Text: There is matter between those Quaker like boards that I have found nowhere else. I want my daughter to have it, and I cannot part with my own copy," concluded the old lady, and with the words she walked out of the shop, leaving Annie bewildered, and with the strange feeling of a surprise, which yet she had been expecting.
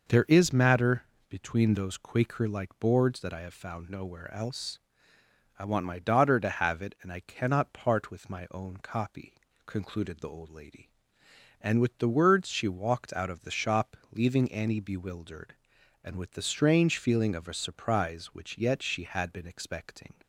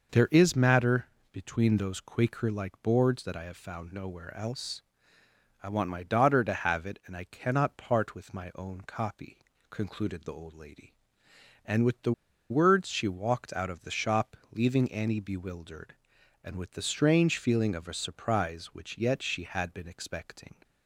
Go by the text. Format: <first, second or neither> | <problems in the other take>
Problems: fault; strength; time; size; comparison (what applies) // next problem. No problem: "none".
first | pauses between "matter" and "between"; slight; at 1.0 s; 0.26 s long; slight in the first // pauses between "the" and "words"; at 12.1 s; 0.38 s long